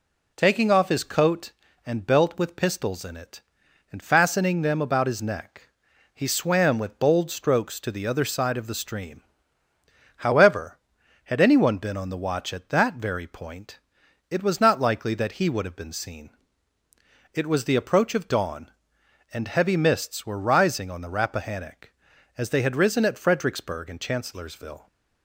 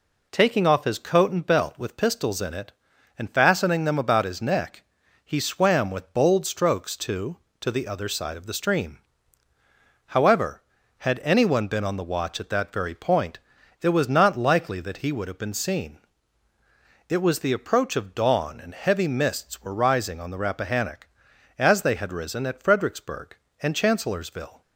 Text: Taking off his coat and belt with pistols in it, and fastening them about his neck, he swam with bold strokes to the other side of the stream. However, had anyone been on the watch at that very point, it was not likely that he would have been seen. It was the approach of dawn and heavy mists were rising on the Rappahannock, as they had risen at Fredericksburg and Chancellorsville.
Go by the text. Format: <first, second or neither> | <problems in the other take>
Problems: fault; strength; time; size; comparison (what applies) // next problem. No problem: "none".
first | says "to" twice; at 7.6 s